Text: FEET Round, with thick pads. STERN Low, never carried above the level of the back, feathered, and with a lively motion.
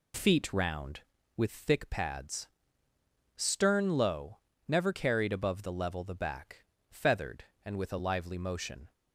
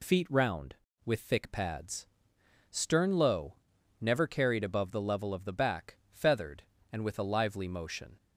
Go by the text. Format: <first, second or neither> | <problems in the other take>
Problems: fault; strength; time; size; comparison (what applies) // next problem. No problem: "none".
second | skips "of"; at 6.0 s